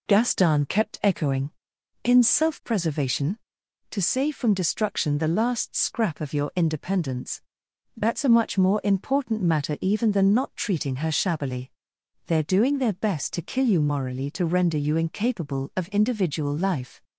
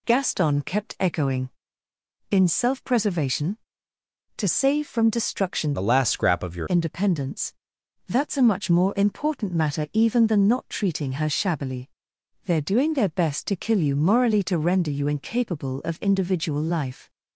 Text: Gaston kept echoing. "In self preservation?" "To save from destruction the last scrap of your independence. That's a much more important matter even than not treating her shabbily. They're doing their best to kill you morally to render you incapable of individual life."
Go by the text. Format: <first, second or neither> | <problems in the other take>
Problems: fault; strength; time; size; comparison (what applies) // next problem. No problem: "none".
first | changes voice from "the" to "your"; from 5.7 to 6.6 s; 0.9 s long